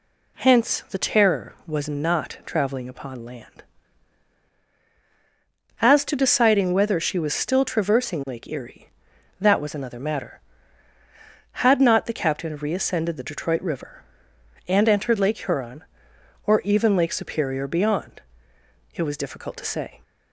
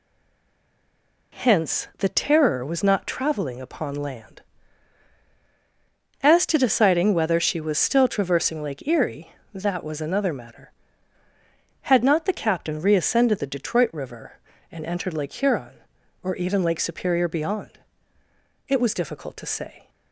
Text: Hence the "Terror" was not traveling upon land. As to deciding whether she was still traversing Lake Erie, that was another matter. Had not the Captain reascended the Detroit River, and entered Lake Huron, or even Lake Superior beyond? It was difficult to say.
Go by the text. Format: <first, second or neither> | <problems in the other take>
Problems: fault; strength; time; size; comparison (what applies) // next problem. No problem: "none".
first | stays silent before the first word; noticeable; until 1.3 s; 1.3 s long